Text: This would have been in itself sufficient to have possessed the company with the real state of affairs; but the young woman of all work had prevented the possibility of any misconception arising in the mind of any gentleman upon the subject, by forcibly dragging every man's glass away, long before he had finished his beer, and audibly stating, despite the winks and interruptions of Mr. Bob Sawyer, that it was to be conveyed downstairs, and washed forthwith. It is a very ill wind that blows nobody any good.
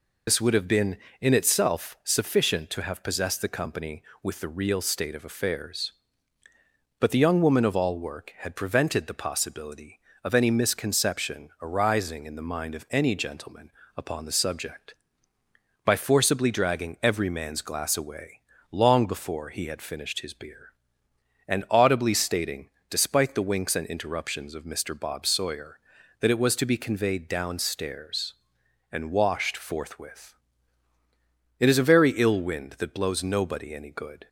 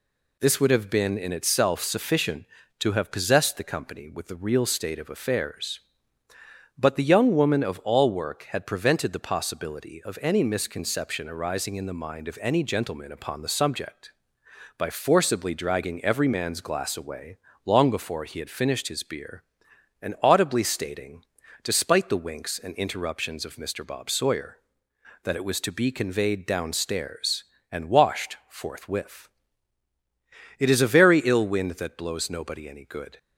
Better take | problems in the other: second | loses the start of "This"; at 0.2 s; 55 ms // pauses between "gentleman" and "upon"; slight; at 13.6 s; 0.26 s long

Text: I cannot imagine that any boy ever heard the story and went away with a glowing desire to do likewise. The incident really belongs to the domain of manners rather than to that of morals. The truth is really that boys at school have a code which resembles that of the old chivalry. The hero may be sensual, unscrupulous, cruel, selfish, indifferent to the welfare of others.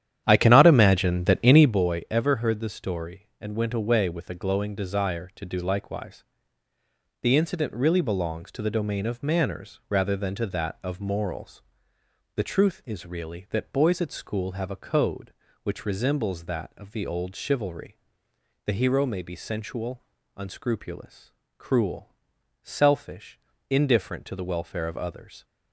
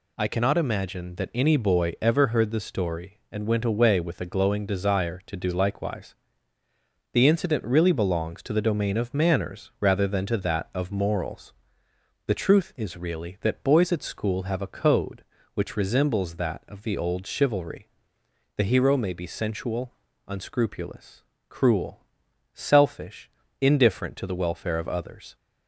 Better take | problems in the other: second | starts louder than the rest; strong; until 1.8 s; 10 dB

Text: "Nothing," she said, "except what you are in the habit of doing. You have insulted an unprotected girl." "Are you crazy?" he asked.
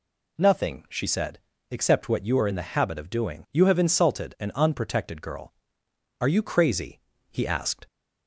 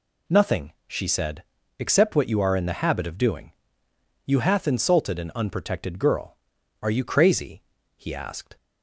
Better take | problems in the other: first | says "hath" for "have"; at 4.3 s

